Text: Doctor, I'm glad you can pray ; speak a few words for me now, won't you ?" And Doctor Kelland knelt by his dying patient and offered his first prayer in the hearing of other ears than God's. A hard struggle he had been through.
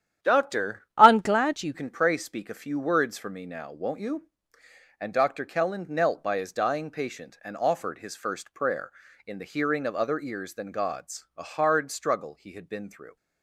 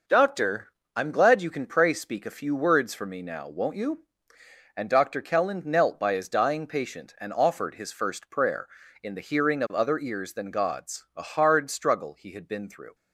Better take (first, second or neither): second